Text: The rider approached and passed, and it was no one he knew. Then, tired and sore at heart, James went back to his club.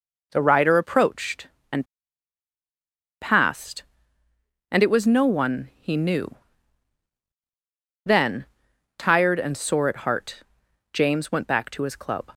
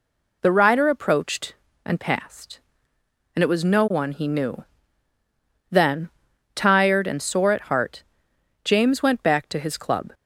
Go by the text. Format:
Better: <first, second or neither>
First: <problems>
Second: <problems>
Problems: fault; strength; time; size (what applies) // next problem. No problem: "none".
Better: second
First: pauses between "and" and "passed"; strong; at 1.8 s; 1.3 s long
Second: none